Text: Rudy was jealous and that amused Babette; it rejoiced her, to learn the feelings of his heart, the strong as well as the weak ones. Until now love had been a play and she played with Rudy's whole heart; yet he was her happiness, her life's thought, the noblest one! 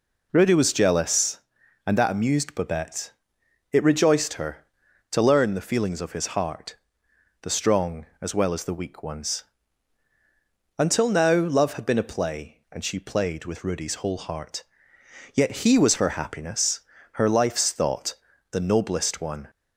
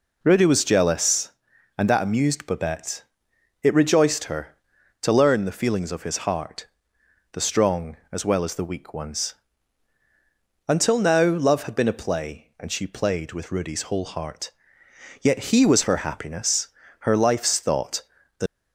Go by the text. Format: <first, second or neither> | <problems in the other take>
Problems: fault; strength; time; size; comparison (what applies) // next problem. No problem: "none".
first | stops before "noblest one"; at 18.4 s